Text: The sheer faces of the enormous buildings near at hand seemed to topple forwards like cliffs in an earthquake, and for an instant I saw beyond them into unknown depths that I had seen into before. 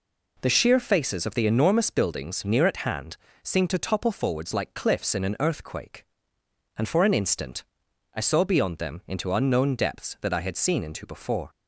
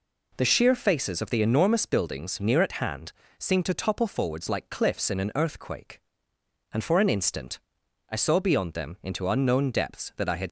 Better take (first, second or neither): first